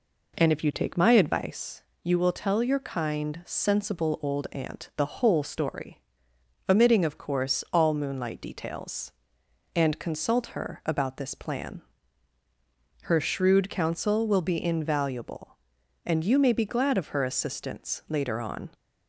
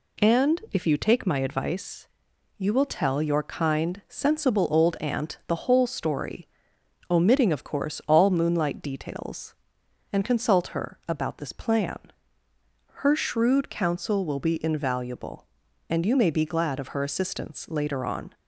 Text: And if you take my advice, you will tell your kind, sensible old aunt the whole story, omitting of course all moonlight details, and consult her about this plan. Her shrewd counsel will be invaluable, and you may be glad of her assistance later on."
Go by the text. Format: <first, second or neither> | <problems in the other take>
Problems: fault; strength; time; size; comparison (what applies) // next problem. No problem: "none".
second | starts louder than the rest; until 1.4 s; 4 dB